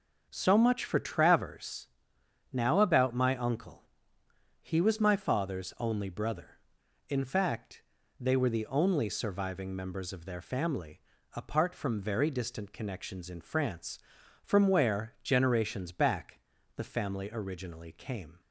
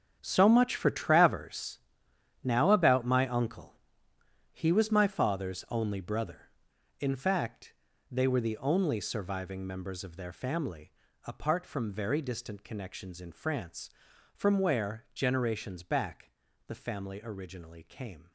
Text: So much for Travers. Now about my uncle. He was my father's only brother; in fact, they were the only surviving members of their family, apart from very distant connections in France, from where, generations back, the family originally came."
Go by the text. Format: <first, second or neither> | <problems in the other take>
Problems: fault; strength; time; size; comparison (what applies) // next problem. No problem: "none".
first | gets quieter; strong; throughout; 13.5 dB